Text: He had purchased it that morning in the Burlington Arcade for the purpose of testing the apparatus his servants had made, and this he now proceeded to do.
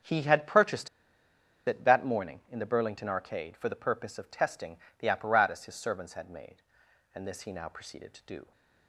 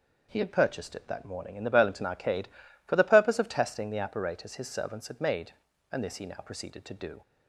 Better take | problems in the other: second | starts louder than the rest; until 1.8 s; 6.5 dB // pauses between "purchased" and "it"; noticeable; at 0.8 s; 0.78 s long // pauses between "testing" and "the"; slight; at 4.7 s; 0.20 s long

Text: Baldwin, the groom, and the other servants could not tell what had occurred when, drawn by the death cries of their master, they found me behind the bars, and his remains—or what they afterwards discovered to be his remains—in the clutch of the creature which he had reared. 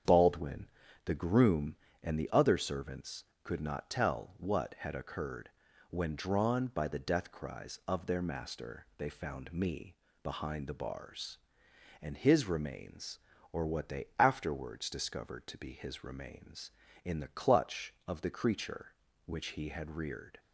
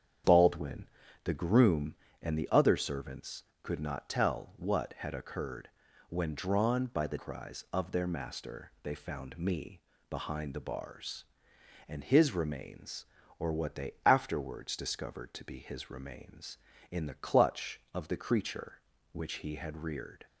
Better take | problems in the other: first | starts louder than the rest; strong; until 1.6 s; 8 dB; strong in the first // pauses between "occurred" and "when"; at 5.6 s; 0.40 s long; also in the first // skips "death"; at 7.1 s // pauses between "me" and "behind"; slight; at 9.8 s; 0.26 s long; slight in the first

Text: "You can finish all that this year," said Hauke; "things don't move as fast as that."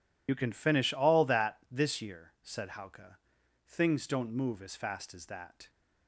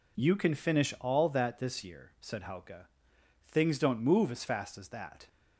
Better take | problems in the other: second | loses the start of "You"; at 0.2 s; 50 ms

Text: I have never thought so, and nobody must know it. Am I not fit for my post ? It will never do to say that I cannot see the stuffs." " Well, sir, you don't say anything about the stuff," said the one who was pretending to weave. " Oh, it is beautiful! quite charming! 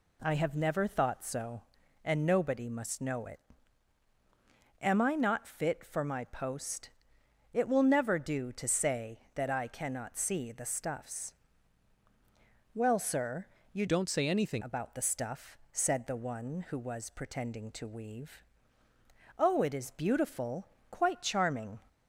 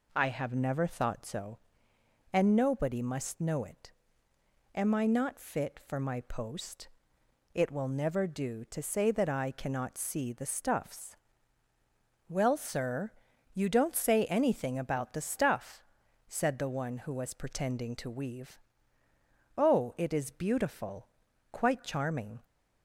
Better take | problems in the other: second | changes voice from "don't" to "anything"; from 13.8 to 14.6 s; 0.8 s long

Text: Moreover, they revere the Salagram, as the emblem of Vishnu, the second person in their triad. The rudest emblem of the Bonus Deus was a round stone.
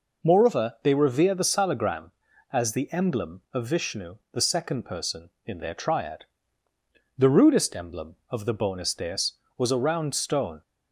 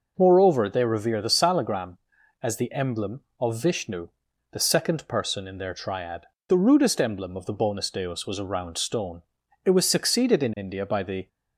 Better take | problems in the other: first | goes on to say "It was succeeded in India by the"; from 9.6 s on; 1.6 s long

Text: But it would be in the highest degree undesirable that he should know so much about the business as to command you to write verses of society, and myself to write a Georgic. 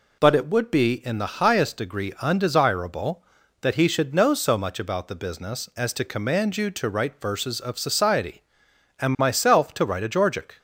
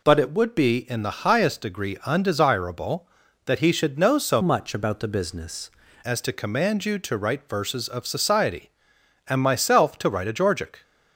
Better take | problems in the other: first | changes voice from "much" to "business"; from 4.4 to 5.7 s; 1.3 s long

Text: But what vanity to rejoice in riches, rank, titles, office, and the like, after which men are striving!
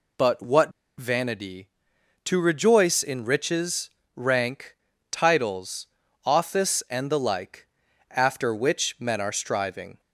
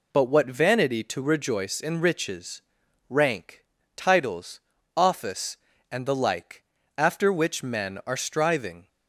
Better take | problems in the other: second | pauses between "what" and "vanity"; slight; at 0.7 s; 0.27 s long

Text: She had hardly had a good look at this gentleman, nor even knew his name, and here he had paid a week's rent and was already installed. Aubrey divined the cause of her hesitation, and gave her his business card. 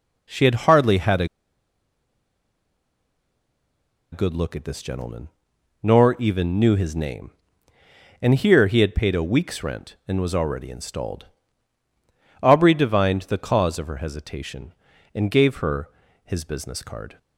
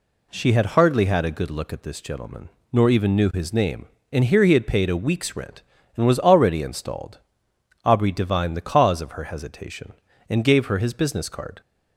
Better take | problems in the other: second | pauses between "a" and "good"; strong; at 1.2 s; 2.8 s long // pauses between "her" and "his"; slight; at 15.8 s; 0.34 s long

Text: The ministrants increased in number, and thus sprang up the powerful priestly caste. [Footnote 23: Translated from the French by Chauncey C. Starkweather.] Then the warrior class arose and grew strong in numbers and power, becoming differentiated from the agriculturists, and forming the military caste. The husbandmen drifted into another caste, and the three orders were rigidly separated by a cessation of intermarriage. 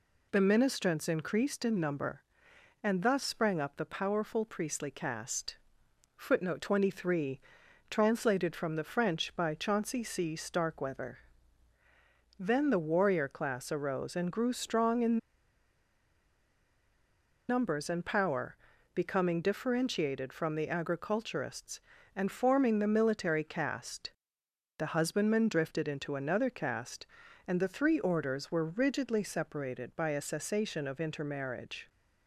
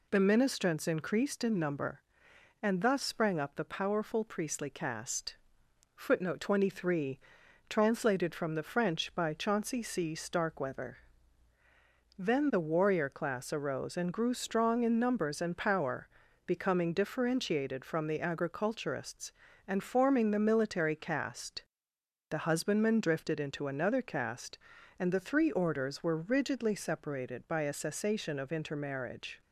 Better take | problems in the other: second | pauses between "in" and "numbers"; strong; at 15.1 s; 2.3 s long

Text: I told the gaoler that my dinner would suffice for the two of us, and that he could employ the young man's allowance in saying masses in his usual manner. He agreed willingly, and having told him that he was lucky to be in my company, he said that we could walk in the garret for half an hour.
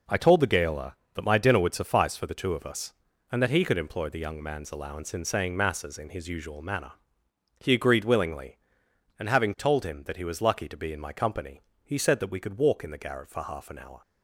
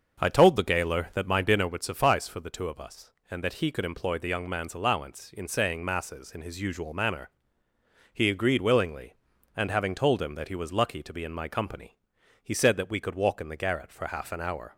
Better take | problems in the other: first | starts louder than the rest; until 1.7 s; 6.5 dB

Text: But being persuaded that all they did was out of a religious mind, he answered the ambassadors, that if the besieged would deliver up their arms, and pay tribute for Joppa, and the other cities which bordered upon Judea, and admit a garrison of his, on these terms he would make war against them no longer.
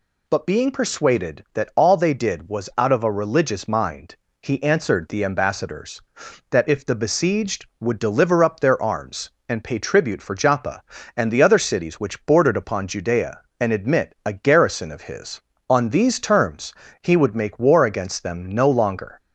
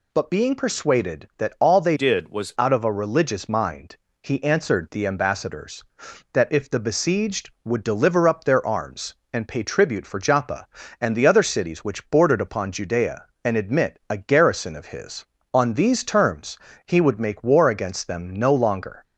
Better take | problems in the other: first | changes voice from "did" to "was"; from 1.9 to 2.5 s; 0.6 s long // pauses between "terms" and "he"; slight; at 16.5 s; 0.28 s long; slight in the first

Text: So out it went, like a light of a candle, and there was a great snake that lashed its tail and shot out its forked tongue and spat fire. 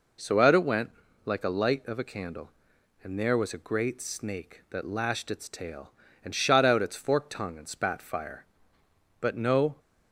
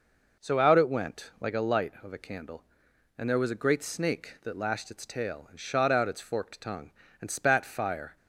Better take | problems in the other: second | goes on to say "But no"; from 9.2 s on; 0.58 s long

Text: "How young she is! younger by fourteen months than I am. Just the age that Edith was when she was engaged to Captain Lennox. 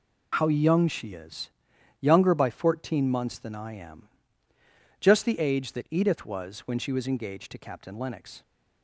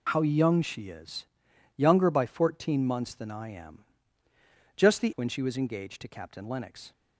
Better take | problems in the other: first | skips "age that Edith was"; at 5.1 s

